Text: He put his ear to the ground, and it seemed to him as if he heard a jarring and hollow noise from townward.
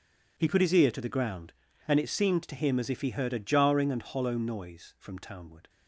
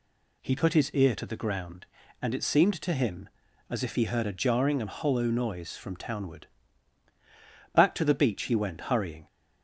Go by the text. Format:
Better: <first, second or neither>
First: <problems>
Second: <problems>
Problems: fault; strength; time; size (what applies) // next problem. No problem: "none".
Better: first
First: none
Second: goes on to say "Back to the beach he went hurrying"; from 7.7 s on; 1.5 s long